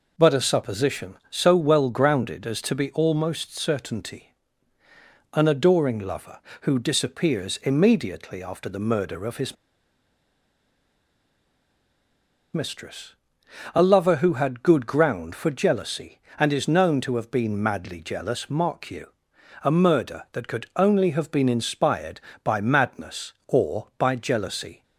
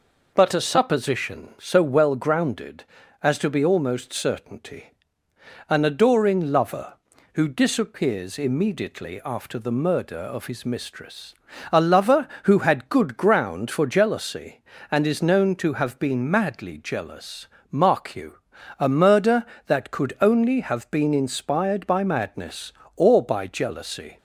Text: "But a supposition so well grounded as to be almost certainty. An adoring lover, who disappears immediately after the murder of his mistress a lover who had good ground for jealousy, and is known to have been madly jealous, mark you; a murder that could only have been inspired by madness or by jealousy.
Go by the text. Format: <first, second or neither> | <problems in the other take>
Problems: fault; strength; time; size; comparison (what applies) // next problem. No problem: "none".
second | pauses between "his" and "mistress"; strong; at 9.5 s; 2.9 s long // pauses between "mistress" and "a"; noticeable; at 13.1 s; 0.58 s long; also in the second